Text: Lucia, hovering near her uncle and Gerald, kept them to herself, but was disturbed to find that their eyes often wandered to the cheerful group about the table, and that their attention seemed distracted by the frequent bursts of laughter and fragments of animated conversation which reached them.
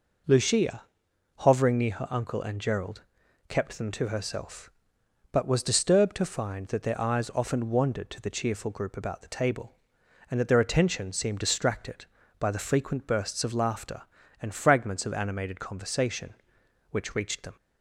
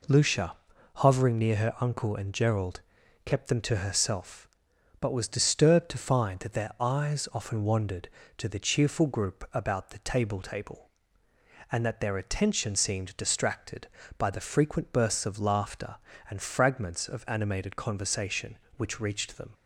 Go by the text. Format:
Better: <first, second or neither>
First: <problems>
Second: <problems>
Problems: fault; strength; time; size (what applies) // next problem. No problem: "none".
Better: first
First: none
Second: says "table" twice; at 10.4 s